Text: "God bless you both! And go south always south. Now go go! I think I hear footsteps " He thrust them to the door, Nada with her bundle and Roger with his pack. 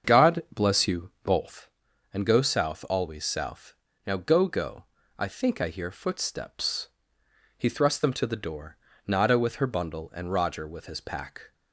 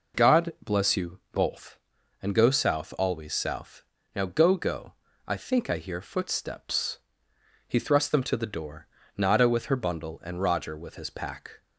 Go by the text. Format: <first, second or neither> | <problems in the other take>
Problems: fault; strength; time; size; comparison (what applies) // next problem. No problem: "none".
second | starts louder than the rest; strong; until 1.5 s; 7 dB